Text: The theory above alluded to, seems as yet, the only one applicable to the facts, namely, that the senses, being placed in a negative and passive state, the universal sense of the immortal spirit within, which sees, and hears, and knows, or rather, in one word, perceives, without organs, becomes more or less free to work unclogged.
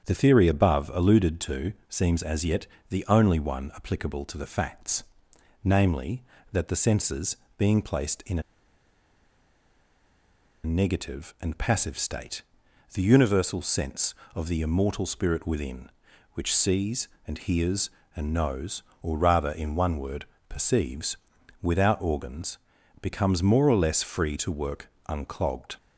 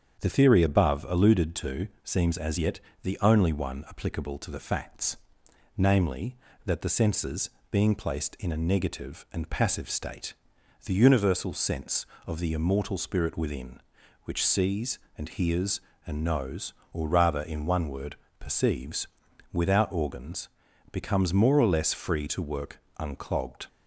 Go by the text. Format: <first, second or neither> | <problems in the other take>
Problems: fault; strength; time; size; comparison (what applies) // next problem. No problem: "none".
second | starts louder than the rest; strong; until 1.0 s; 7.5 dB; strong in the second // pauses between "a" and "negative"; strong; at 8.4 s; 2.2 s long // pauses between "work" and "unclogged"; slight; at 24.8 s; 0.20 s long; slight in the second